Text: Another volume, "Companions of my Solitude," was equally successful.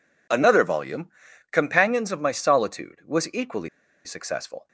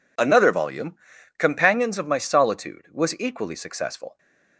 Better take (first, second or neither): second